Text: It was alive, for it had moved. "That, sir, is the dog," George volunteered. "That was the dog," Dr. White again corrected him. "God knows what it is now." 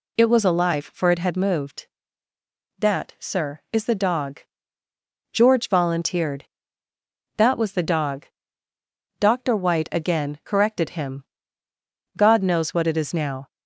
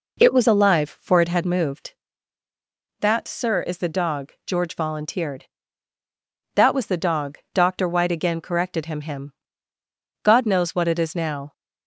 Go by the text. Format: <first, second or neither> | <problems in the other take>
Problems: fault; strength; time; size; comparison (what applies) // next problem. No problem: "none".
first | says "him" twice; at 9.0 s